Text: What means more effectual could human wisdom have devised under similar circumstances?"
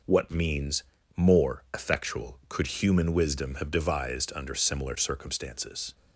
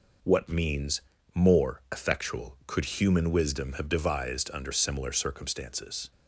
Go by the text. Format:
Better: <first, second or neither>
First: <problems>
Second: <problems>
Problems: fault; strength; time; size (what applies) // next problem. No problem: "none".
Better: neither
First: pauses between "means" and "more"; slight; at 0.8 s; 0.34 s long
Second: pauses between "means" and "more"; slight; at 1.0 s; 0.34 s long